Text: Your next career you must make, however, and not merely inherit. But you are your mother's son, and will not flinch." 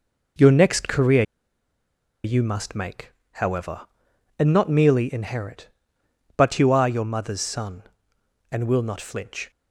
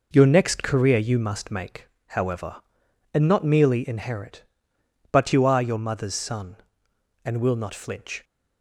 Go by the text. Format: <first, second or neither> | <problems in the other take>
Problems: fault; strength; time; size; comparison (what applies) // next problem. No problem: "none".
second | pauses between "career" and "you"; at 1.2 s; 1.0 s long